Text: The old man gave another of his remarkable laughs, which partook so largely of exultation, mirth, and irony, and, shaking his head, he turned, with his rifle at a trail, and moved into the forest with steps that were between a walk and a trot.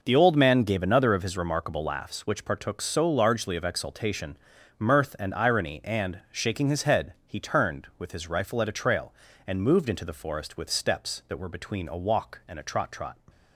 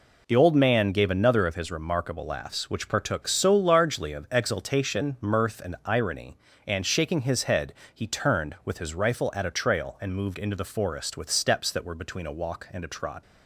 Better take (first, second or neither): second